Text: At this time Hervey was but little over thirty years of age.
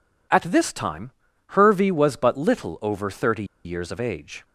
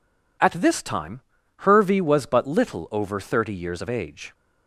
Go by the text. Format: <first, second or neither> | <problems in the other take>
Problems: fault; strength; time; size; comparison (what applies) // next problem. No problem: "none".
second | pauses between "time" and "Hervey"; at 1.1 s; 0.38 s long; also in the second // pauses between "thirty" and "years"; slight; at 3.4 s; 0.20 s long